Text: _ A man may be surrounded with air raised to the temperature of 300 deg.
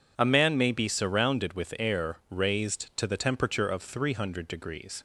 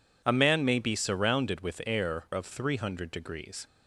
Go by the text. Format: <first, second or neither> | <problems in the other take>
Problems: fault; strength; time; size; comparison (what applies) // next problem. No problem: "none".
first | skips "raised to the temperature"; at 2.2 s